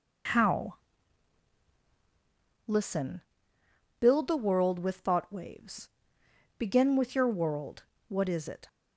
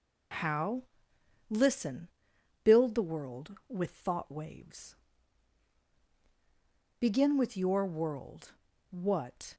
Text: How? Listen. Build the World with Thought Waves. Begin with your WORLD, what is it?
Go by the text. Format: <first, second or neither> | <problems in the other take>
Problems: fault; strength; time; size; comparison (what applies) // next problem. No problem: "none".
first | stops before "is it"; at 9.5 s